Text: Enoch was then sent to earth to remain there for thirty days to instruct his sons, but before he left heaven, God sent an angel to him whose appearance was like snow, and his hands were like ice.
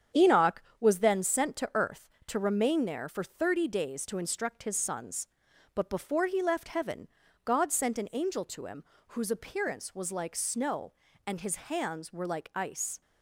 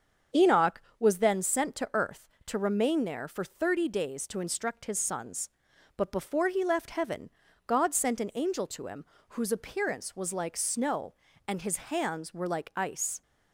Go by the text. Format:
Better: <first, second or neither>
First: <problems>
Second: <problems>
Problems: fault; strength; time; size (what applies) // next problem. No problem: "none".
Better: second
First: gets quieter; throughout; 6.5 dB // starts louder than the rest; strong; until 1.3 s; 8 dB // pauses between "him" and "whose"; slight; at 8.8 s; 0.26 s long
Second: starts louder than the rest; until 1.5 s; 7 dB // pauses between "him" and "whose"; slight; at 9.0 s; 0.26 s long